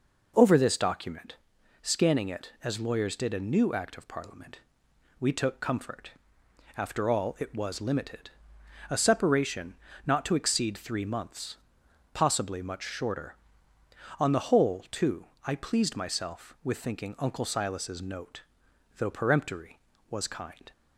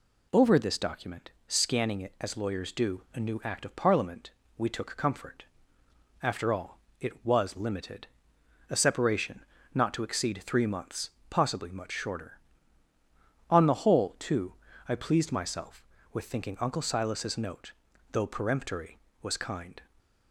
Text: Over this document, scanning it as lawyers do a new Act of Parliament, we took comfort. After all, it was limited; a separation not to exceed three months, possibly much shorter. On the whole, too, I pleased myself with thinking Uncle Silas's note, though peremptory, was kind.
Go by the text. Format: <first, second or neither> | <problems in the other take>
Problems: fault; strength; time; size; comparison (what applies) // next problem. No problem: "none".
second | says "did" for "do"; at 3.1 s // pauses between "separation" and "not"; slight; at 9.7 s; 0.32 s long; slight in the second